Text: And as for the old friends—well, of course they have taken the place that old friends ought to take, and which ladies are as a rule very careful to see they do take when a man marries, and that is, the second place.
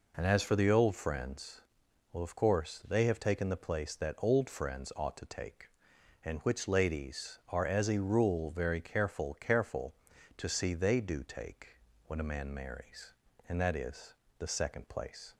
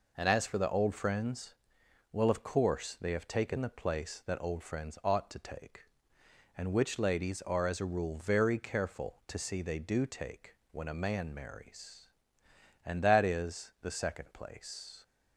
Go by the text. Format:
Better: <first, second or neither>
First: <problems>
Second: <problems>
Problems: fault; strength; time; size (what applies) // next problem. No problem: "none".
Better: second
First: says "careful" twice; at 9.3 s // pauses between "take" and "when"; slight; at 11.7 s; 0.30 s long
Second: pauses between "take" and "when"; slight; at 10.5 s; 0.18 s long